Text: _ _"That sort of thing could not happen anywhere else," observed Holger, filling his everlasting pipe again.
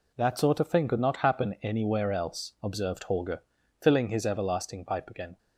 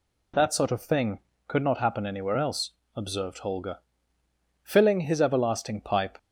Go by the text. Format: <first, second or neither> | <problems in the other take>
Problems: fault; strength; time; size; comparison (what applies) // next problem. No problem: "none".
first | stops before "again"; at 6.1 s